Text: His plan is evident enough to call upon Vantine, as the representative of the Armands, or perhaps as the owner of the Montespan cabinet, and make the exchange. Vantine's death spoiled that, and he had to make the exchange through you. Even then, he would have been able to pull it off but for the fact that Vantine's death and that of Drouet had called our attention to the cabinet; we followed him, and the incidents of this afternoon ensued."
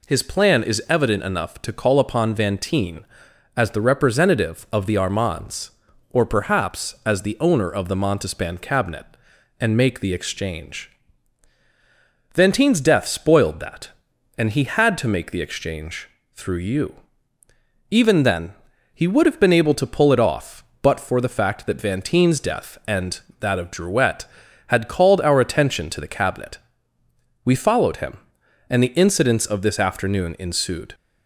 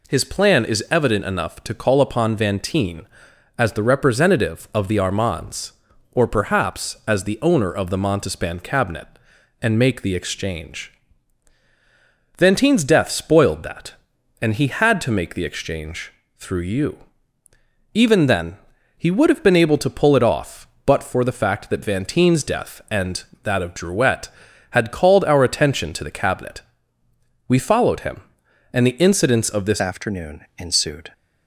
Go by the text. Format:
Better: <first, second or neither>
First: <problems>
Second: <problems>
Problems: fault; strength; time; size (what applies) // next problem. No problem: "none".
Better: first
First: pauses between "exchange" and "through"; slight; at 16.0 s; 0.26 s long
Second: pauses between "exchange" and "through"; slight; at 16.1 s; 0.26 s long // changes voice at "afternoon"; from 29.7 s on; 1.4 s long